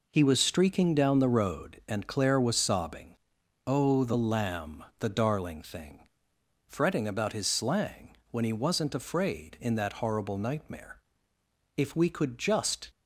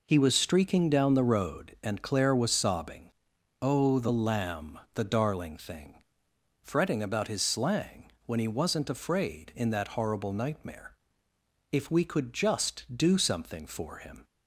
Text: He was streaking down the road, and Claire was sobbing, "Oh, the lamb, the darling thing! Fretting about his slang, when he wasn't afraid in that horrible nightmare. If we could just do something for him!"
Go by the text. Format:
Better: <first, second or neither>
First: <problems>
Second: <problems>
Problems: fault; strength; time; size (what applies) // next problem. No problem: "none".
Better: second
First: stops before "do something for him"; at 12.8 s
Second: none